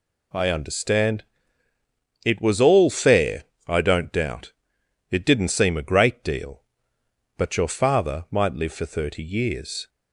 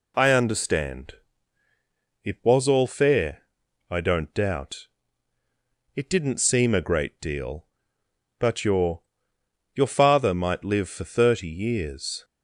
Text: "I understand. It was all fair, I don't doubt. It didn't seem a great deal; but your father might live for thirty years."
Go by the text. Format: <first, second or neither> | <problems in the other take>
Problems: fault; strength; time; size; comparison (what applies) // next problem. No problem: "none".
first | says "your" twice; at 9.7 s